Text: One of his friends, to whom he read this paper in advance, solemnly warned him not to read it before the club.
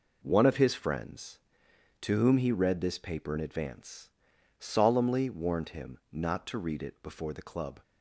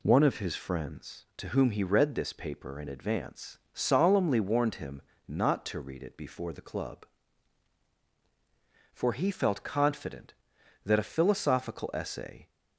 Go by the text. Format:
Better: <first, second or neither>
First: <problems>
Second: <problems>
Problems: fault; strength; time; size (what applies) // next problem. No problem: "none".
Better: first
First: none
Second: pauses between "him" and "not"; slight; at 4.9 s; 0.28 s long // goes on to say "For he felt confident that a philosophical essay"; strong; from 8.9 s on; 3.5 s long